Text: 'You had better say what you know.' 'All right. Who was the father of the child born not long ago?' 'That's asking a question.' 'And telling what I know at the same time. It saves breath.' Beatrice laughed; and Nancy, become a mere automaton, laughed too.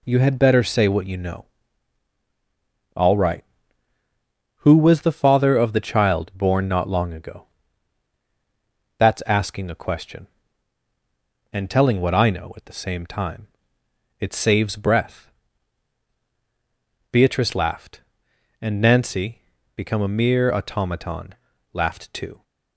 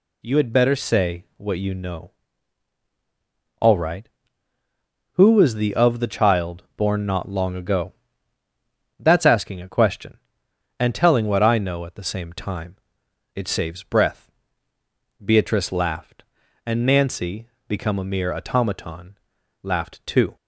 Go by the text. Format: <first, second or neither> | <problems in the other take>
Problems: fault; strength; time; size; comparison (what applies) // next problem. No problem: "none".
first | skips "father"; at 5.7 s